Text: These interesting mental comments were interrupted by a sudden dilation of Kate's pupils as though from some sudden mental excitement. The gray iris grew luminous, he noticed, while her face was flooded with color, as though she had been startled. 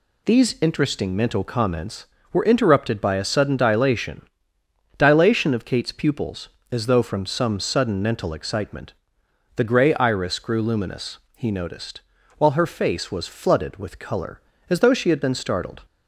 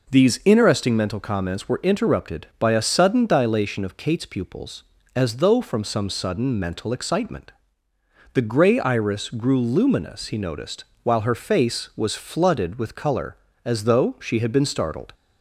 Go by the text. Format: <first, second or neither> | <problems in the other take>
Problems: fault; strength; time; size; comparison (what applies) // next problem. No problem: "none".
second | says "dilation" twice; at 4.9 s